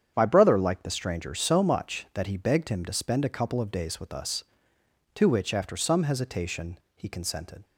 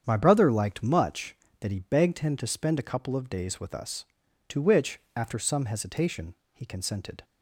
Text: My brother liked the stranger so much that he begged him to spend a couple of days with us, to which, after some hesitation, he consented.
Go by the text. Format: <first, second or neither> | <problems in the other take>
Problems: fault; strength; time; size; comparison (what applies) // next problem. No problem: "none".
first | starts louder than the rest; strong; until 1.0 s; 8 dB; strong in the first // skips "the stranger so"; at 0.8 s